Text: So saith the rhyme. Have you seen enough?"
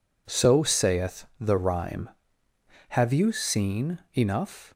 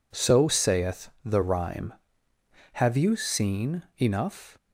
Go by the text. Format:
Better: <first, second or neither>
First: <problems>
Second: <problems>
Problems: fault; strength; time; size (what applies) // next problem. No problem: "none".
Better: neither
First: pauses between "saith" and "the"; slight; at 1.2 s; 0.15 s long // pauses between "seen" and "enough"; slight; at 3.9 s; 0.18 s long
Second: pauses between "saith" and "the"; slight; at 1.0 s; 0.16 s long // pauses between "seen" and "enough"; slight; at 3.8 s; 0.18 s long